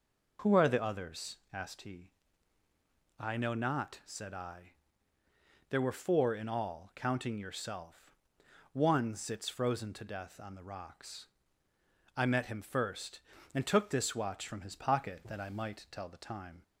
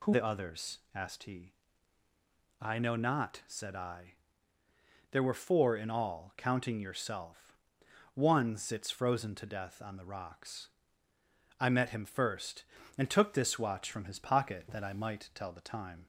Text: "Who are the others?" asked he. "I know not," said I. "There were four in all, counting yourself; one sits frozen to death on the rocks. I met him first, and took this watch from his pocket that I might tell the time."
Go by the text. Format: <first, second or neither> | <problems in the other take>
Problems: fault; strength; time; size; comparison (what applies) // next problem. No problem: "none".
first | skips "are"; at 0.1 s